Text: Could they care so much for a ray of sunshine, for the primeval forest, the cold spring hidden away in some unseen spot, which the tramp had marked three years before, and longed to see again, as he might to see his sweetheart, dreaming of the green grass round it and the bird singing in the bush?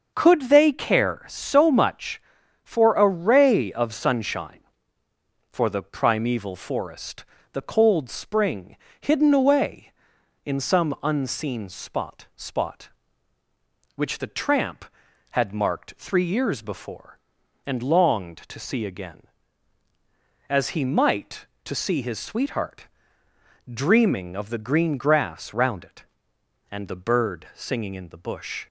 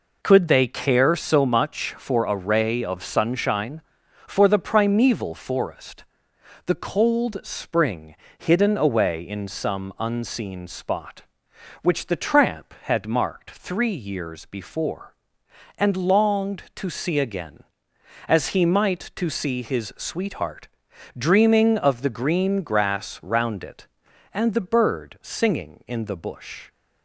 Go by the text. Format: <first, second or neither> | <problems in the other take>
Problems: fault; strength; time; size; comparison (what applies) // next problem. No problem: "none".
second | starts louder than the rest; until 1.1 s; 6.5 dB // pauses between "spring" and "hidden"; slight; at 8.7 s; 0.24 s long; slight in the second // says "spot" twice; at 12.3 s